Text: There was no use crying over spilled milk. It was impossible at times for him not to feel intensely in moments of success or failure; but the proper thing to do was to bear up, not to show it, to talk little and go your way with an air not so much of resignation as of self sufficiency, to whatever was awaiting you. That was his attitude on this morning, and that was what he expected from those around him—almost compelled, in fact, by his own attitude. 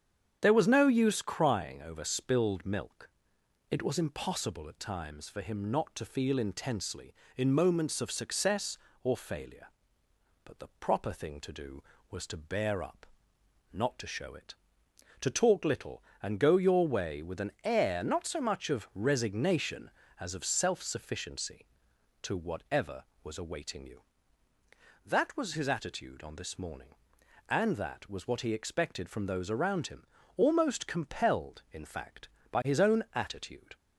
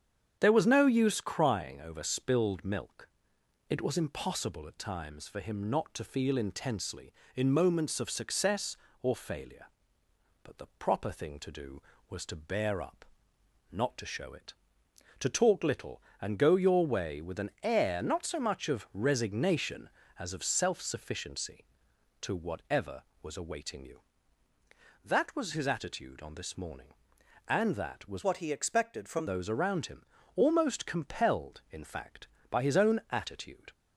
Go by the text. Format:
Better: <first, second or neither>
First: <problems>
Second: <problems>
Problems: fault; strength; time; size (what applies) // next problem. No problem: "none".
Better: first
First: starts louder than the rest; strong; until 1.4 s; 8 dB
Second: starts louder than the rest; strong; until 1.4 s; 8 dB // changes voice from "what" to "from"; from 28.2 to 29.2 s; 1.0 s long